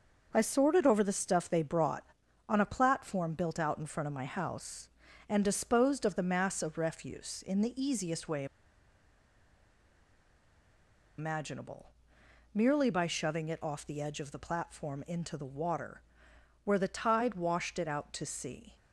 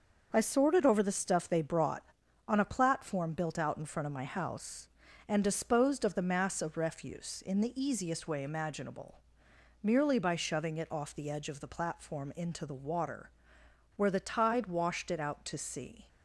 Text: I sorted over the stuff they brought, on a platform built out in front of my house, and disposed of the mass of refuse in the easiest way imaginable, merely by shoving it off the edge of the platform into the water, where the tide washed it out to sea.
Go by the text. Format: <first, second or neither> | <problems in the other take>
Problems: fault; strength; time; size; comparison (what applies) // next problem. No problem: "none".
second | starts louder than the rest; until 1.3 s; 6.5 dB; also in the second // pauses between "way" and "imaginable"; strong; at 8.4 s; 2.7 s long